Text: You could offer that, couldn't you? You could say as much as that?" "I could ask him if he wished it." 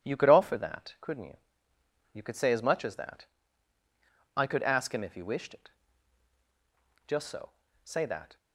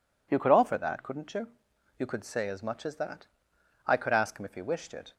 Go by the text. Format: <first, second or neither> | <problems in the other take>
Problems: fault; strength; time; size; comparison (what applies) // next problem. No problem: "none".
second | goes on to say "Just so Say that"; noticeable; from 7.0 s on; 1.2 s long